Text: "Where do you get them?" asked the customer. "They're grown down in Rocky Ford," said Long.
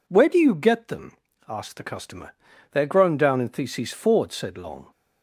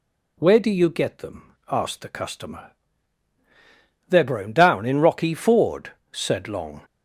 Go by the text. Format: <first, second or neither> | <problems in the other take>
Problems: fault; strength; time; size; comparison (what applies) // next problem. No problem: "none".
second | says "Theses" for "Rocky"; at 3.4 s